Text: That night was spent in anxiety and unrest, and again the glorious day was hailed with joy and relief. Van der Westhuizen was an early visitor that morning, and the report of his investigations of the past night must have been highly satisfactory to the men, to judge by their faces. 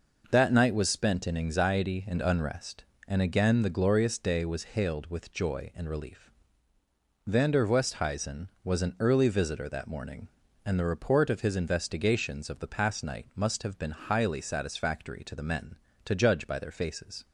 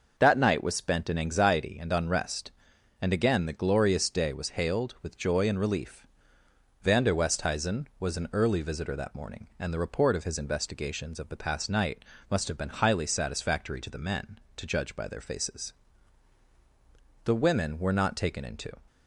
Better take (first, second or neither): first